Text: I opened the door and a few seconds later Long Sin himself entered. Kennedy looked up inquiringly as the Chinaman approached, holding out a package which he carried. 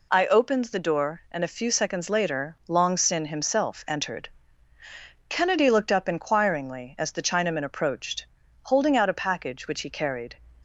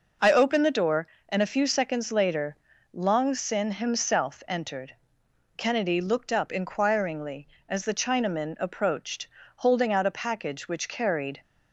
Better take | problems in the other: first | pauses between "later" and "Long"; slight; at 2.5 s; 0.34 s long // skips "he"; at 10.8 s

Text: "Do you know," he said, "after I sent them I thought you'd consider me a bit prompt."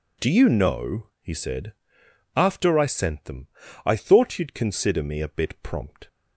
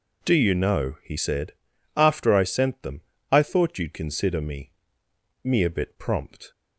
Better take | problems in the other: first | pauses between "them" and "I"; slight; at 2.9 s; 0.32 s long; also in the first // says "me" twice; at 5.4 s

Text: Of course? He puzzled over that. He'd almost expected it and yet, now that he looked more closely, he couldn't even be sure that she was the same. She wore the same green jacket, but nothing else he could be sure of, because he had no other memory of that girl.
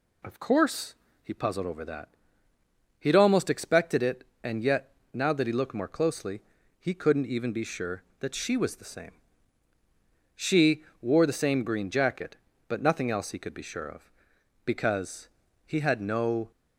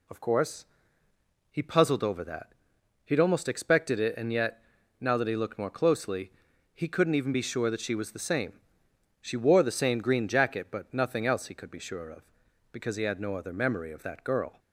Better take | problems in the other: second | pauses between "She" and "wore"; slight; at 10.8 s; 0.18 s long // pauses between "because" and "he"; slight; at 15.2 s; 0.36 s long // stops before "other memory of that girl"; at 16.5 s

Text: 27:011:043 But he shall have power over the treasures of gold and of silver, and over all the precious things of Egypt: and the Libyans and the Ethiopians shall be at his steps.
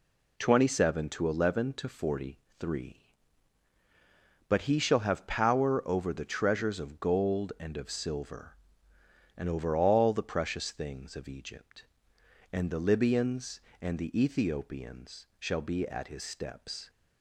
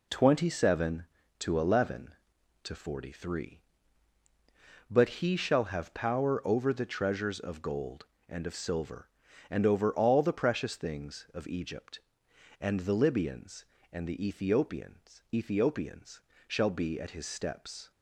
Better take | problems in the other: first | says "Ethiopians" twice; at 15.3 s

